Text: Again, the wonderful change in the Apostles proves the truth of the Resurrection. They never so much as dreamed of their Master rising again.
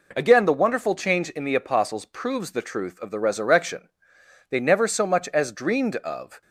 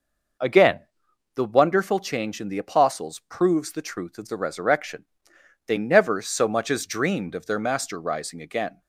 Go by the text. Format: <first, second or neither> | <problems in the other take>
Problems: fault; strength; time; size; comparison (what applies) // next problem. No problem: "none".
second | stops before "their Master rising again"; at 6.4 s